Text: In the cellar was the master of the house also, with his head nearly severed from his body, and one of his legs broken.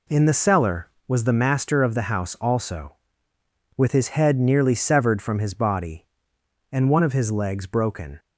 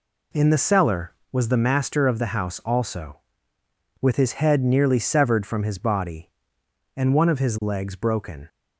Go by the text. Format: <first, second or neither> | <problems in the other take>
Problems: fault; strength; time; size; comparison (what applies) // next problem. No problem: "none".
neither | none